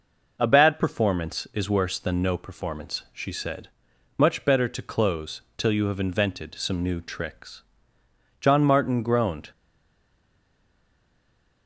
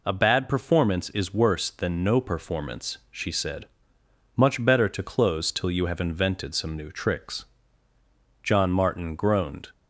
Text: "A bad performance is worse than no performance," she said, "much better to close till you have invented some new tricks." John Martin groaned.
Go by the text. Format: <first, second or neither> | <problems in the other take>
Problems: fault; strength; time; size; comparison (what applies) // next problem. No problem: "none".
second | pauses between "close" and "till"; slight; at 5.4 s; 0.16 s long // stays silent after the last word; from 9.5 s on; 2.1 s long